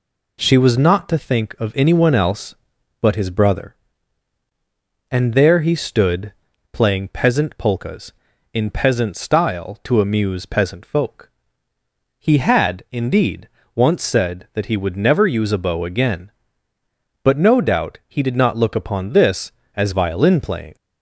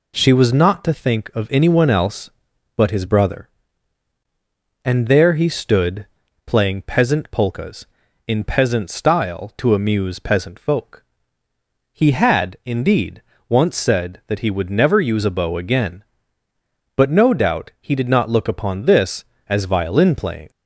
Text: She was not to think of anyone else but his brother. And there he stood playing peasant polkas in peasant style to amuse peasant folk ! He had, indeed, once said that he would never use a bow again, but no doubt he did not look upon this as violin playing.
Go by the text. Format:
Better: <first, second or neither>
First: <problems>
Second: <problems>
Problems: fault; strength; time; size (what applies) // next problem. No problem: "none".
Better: neither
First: pauses between "stood" and "playing"; at 6.3 s; 0.40 s long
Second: pauses between "stood" and "playing"; at 6.0 s; 0.40 s long